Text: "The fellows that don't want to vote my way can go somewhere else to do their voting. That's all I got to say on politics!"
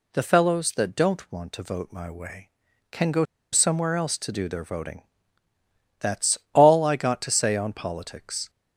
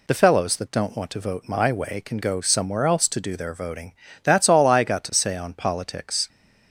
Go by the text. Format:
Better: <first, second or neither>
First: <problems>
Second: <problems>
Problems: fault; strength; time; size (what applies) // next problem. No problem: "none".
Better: second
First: pauses between "go" and "somewhere"; slight; at 3.2 s; 0.29 s long // pauses between "That's" and "all"; slight; at 6.3 s; 0.16 s long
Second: none